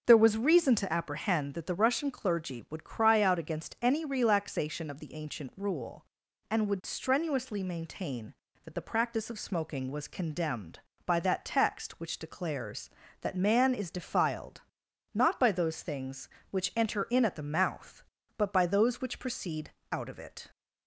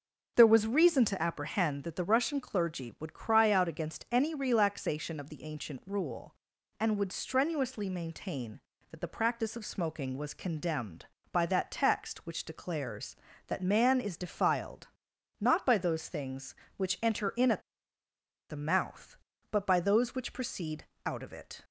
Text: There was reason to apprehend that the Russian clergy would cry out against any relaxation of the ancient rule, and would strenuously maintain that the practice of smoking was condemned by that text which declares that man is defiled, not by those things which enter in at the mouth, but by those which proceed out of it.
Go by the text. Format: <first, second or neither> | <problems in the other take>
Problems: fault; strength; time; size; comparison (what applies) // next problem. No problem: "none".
first | starts louder than the rest; until 1.3 s; 6.5 dB; also in the first // pauses between "at" and "the"; noticeable; at 17.6 s; 0.87 s long // pauses between "proceed" and "out"; slight; at 20.8 s; 0.20 s long; slight in the first